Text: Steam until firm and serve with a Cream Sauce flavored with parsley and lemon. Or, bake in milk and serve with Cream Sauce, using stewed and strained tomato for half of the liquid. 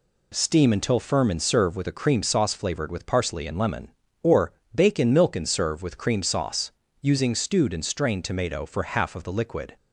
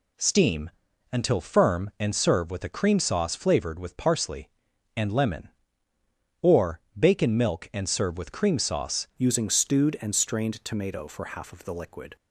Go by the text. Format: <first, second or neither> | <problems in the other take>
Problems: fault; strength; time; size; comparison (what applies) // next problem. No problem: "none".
first | pauses between "Steam" and "until"; at 0.7 s; 0.42 s long // changes voice at "using"; from 9.1 s on; 3.0 s long